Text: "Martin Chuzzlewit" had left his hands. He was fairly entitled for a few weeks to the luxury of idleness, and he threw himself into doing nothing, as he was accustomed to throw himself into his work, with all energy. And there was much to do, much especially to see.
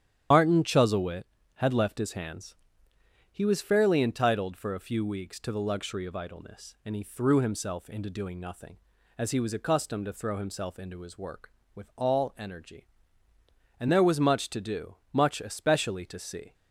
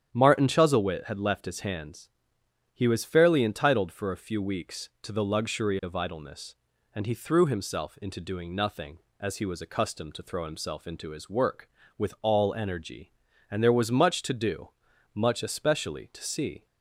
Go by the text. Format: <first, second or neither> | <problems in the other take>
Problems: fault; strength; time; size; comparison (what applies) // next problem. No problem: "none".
second | loses the start of "Martin"; at 0.3 s; 65 ms // starts louder than the rest; strong; until 1.6 s; 10 dB; strong in the second